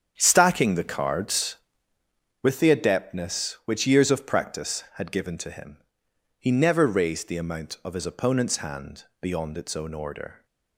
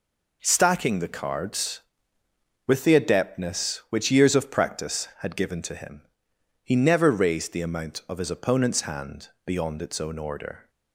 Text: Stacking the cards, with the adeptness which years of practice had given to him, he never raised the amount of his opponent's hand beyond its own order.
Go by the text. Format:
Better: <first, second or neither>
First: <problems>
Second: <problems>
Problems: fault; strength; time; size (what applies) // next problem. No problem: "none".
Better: second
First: starts louder than the rest; strong; until 1.9 s; 8 dB // pauses between "hand" and "beyond"; slight; at 9.0 s; 0.16 s long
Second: pauses between "hand" and "beyond"; slight; at 9.2 s; 0.16 s long